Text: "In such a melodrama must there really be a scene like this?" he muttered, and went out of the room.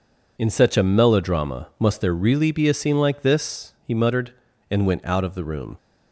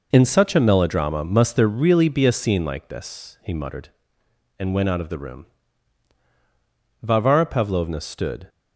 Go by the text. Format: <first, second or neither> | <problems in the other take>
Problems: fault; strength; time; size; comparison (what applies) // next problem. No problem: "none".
first | goes on to say "Varvara Pavlovna stood"; from 7.0 s on; 1.4 s long